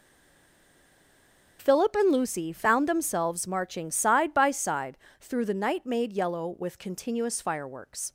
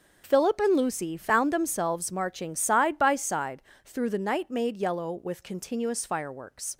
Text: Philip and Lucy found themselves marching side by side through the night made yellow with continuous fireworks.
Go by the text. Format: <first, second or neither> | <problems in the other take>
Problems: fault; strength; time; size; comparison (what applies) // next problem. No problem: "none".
second | stays silent before the first word; noticeable; until 1.5 s; 1.5 s long // starts louder than the rest; noticeable; until 2.6 s; 6 dB; noticeable in the second // pauses between "side" and "through"; slight; at 4.9 s; 0.24 s long; slight in the second